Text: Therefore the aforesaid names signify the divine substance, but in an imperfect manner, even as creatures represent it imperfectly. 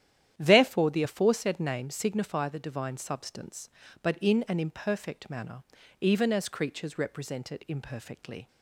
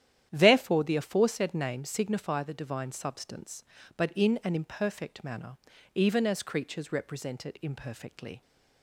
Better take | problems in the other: neither | starts louder than the rest; strong; the same in both

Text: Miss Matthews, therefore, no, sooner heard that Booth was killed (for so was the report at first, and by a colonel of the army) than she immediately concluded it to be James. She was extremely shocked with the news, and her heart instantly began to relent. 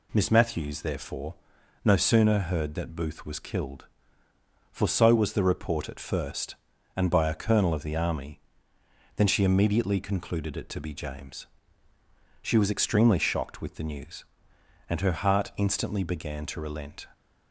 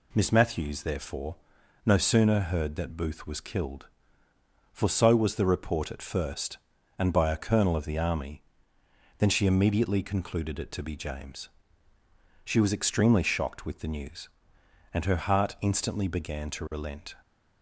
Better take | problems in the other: neither | none

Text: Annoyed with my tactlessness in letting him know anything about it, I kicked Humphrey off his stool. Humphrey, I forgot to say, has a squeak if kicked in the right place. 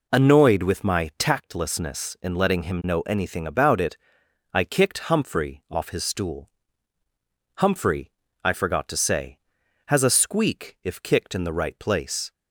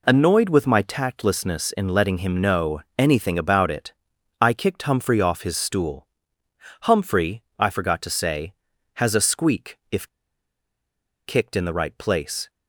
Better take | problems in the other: first | pauses between "know" and "anything"; slight; at 2.8 s; 0.16 s long // pauses between "if" and "kicked"; at 10.0 s; 1.2 s long

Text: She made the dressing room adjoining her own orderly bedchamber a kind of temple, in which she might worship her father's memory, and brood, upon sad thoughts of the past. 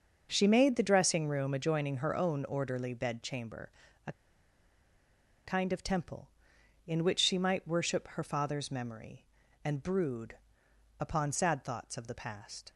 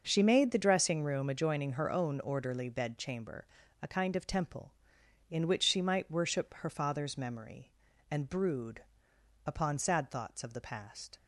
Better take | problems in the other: second | starts louder than the rest; noticeable; until 1.3 s; 6 dB; noticeable in the second // pauses between "bedchamber" and "a"; slight; at 3.7 s; 0.34 s long; slight in the second // pauses between "a" and "kind"; strong; at 4.1 s; 1.3 s long

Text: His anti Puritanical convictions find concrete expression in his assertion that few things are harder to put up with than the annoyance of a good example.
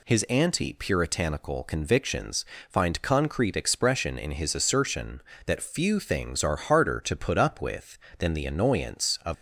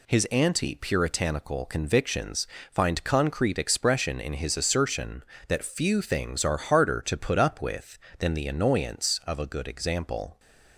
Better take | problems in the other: second | pauses between "convictions" and "find"; slight; at 2.4 s; 0.24 s long; slight in the second // stops before "a good example"; at 9.3 s

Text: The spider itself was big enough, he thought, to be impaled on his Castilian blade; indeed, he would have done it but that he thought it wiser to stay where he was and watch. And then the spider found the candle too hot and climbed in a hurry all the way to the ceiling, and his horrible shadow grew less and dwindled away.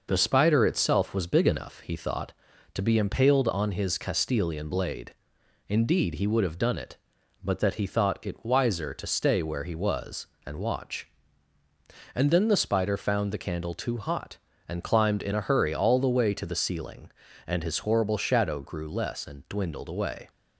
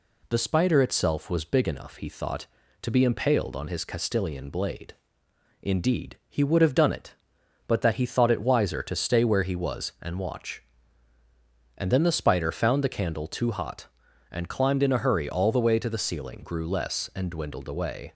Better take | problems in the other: first | skips "and his horrible shadow"; at 16.4 s

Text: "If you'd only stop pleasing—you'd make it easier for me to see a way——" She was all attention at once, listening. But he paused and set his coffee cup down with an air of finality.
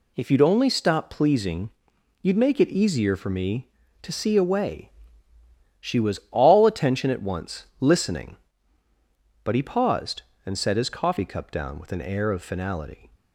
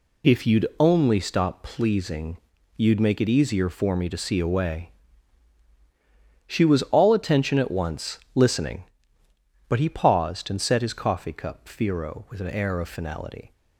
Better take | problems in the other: first | says "firo" for "down"; at 11.6 s

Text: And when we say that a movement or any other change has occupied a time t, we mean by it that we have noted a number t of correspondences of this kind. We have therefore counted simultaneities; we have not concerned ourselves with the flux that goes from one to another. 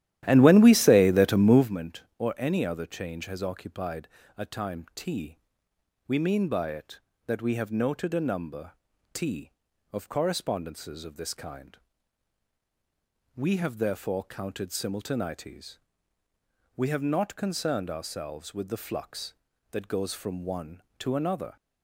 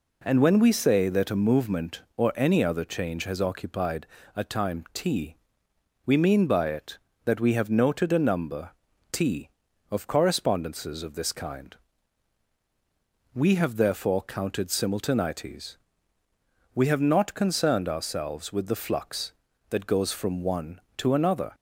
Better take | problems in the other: second | starts louder than the rest; strong; until 1.7 s; 12.5 dB // pauses between "occupied" and "a"; slight; at 4.0 s; 0.30 s long; slight in the second // pauses between "number" and "t"; at 8.7 s; 0.40 s long; also in the second

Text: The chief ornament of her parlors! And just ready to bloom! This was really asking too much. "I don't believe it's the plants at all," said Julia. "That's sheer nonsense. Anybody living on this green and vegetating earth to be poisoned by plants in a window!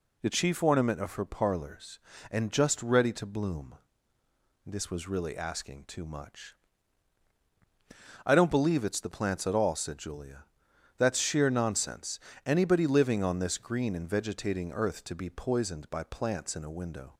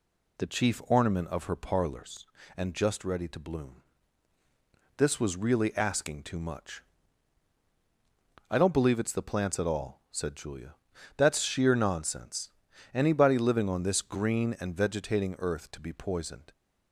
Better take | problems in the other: first | stops before "by plants in a window"; at 16.5 s

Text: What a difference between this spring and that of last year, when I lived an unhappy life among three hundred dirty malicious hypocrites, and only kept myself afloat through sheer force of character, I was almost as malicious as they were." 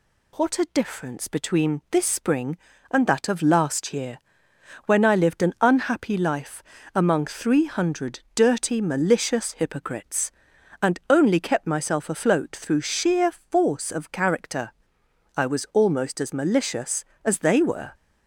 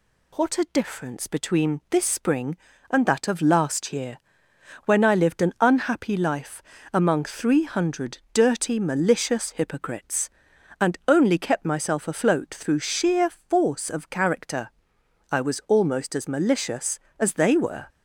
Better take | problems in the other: neither | pauses between "life" and "among"; slight; the same in both // pauses between "hundred" and "dirty"; slight; the same in both

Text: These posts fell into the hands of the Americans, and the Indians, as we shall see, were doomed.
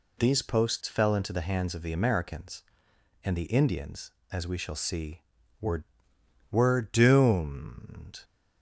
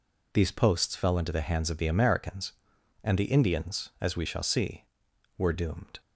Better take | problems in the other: second | says "were" twice; at 6.4 s

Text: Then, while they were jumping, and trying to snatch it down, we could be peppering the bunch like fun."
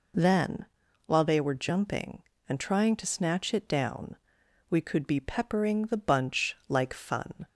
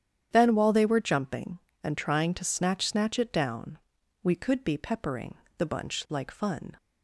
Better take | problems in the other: first | starts louder than the rest; strong; until 1.3 s; 9.5 dB // says "snatch" twice; at 2.8 s // pauses between "peppering" and "the"; slight; at 5.3 s; 0.22 s long

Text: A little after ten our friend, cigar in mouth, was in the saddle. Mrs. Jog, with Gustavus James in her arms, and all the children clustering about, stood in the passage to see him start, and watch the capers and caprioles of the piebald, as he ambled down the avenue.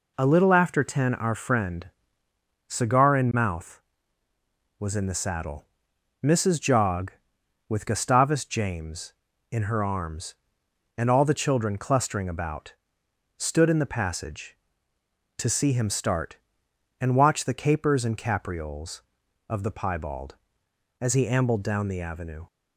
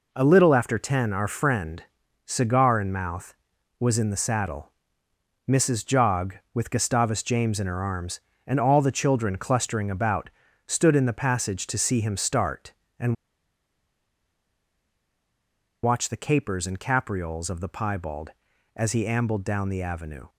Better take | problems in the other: first | pauses between "and" and "watch"; strong; at 13.1 s; 2.6 s long

